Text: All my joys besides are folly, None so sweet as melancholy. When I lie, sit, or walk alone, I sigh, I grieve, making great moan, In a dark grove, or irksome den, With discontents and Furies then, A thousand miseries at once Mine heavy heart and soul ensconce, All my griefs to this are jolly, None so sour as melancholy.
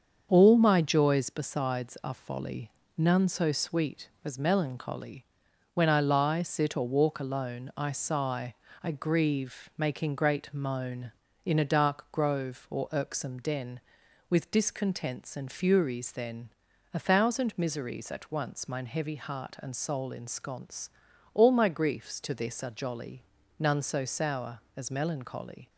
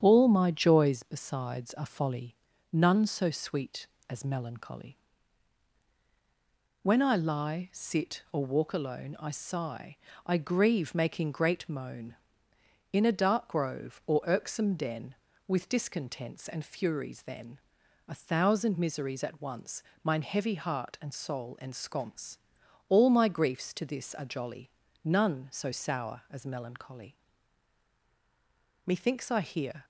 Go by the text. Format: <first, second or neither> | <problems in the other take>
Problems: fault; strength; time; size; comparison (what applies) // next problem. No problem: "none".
first | starts louder than the rest; strong; until 1.0 s; 9 dB; also in the first // pauses between "once" and "Mine"; slight; at 19.8 s; 0.20 s long // goes on to say "Methinks I hear"; noticeable; from 28.8 s on; 0.98 s long